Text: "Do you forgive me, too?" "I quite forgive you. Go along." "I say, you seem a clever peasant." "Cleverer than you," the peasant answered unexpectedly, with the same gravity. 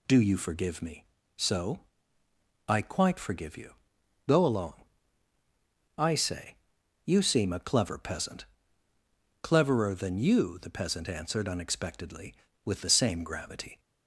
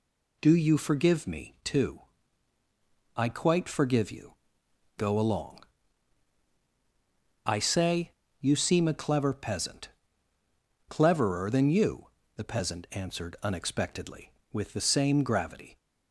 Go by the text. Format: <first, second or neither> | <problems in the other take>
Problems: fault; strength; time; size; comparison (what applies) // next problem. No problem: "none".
second | says "so" for "too"; at 1.3 s